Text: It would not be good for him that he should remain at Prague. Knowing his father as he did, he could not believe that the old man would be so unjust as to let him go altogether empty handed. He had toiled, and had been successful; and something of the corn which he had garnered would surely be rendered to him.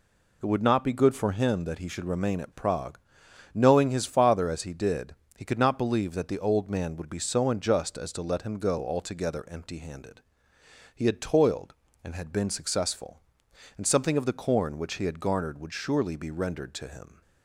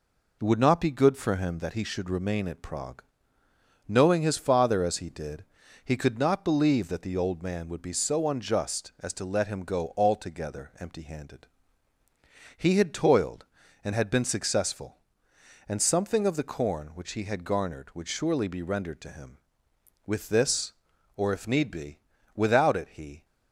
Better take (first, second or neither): first